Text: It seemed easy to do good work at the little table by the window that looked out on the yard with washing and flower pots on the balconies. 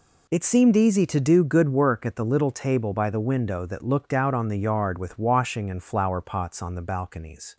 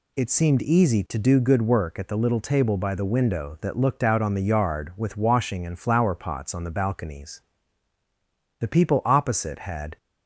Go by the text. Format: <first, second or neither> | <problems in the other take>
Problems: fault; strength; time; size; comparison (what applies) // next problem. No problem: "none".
first | goes on to say "The people opposite had"; from 8.5 s on; 1.3 s long